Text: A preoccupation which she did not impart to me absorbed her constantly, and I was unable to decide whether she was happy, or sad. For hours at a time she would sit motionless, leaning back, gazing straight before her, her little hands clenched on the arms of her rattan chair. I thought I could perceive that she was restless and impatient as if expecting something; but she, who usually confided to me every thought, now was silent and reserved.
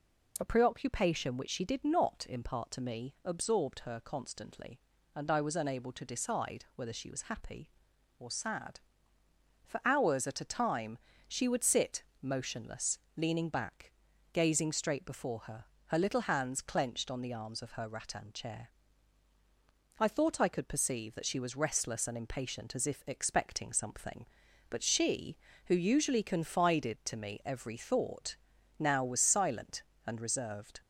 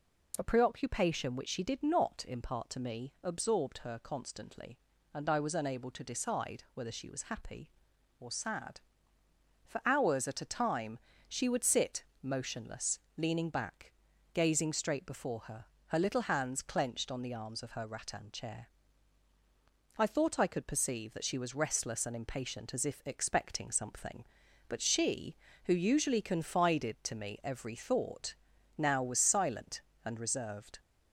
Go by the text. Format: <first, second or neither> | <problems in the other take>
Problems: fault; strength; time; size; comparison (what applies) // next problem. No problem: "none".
neither | pauses between "time" and "she"; slight; the same in both // pauses between "sit" and "motionless"; slight; the same in both